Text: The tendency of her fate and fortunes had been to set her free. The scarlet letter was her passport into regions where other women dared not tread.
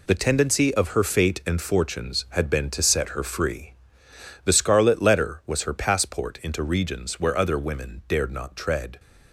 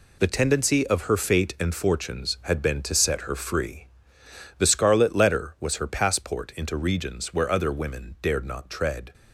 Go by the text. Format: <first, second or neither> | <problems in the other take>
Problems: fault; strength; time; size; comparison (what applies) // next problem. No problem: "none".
neither | none